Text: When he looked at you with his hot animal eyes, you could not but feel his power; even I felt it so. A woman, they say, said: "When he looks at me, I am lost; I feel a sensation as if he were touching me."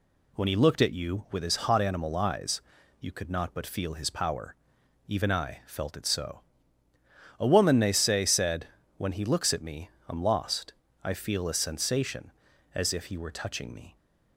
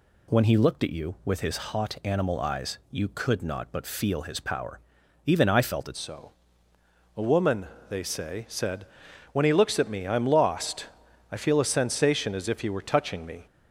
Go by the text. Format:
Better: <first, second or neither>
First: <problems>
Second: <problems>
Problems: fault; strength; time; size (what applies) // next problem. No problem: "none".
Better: first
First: none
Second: changes voice at "so"; from 5.9 s on; 7.5 s long